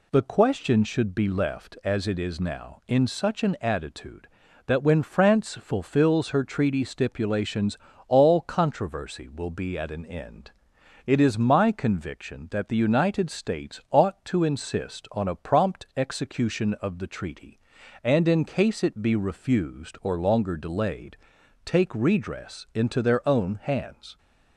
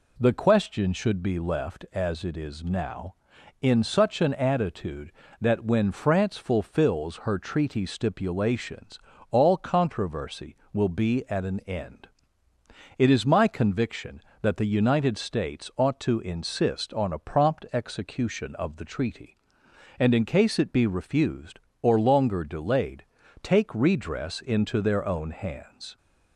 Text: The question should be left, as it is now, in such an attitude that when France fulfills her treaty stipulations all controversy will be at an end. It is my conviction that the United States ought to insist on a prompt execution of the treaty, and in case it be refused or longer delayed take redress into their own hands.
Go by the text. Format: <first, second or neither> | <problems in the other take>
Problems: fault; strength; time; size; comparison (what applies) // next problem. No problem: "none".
neither | pauses between "stipulations" and "all"; slight; the same in both // pauses between "delayed" and "take"; the same in both